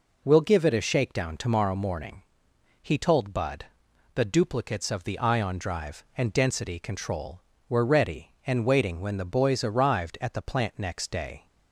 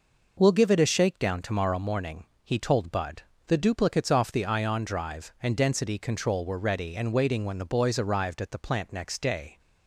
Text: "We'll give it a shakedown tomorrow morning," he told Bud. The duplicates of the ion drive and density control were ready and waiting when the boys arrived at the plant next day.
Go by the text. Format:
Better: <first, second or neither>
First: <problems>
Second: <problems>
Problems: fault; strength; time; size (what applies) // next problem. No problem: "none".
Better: first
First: none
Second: says "off" for "of"; at 4.1 s